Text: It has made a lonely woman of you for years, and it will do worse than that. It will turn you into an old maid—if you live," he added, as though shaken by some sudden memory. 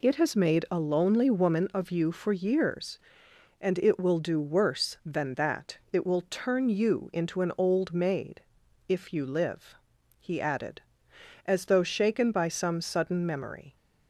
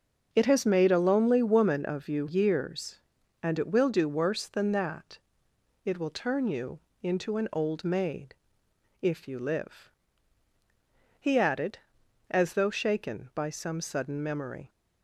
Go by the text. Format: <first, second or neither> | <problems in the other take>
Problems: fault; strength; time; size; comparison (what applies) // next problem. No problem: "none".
first | starts louder than the rest; noticeable; until 1.3 s; 6 dB // skips "for"; at 2.2 s // pauses between "you" and "into"; slight; at 6.7 s; 0.22 s long